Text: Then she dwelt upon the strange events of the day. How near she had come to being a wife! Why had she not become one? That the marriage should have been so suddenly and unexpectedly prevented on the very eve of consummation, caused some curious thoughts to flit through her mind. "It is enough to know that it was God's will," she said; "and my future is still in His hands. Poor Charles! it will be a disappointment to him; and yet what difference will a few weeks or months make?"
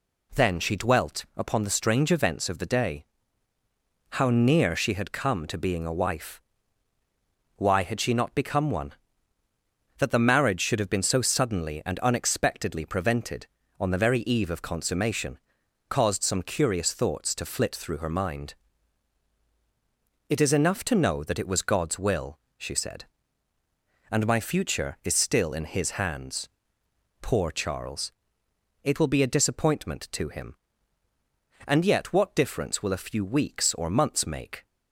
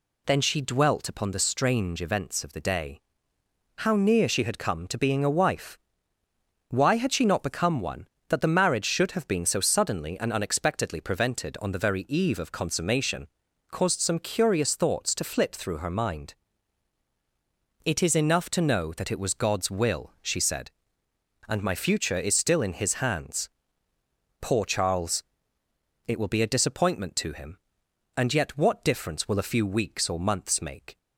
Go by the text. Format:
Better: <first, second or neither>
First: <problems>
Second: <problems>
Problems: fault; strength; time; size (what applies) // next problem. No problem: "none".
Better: neither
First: none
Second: none